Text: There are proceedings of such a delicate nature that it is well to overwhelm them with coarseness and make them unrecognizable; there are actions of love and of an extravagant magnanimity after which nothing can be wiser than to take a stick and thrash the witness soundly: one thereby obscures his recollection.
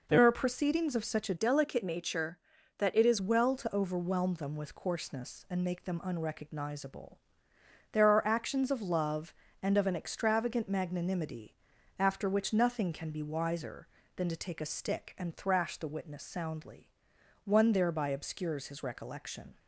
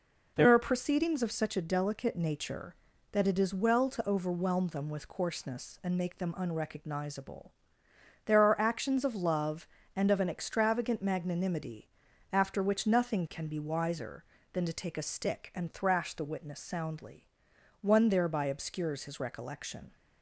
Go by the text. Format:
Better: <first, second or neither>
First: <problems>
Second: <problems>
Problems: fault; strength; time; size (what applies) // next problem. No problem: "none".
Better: second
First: changes voice from "delicate" to "is"; from 1.3 to 3.1 s; 1.8 s long // pauses between "magnanimity" and "after"; at 11.5 s; 0.42 s long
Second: pauses between "magnanimity" and "after"; at 11.8 s; 0.42 s long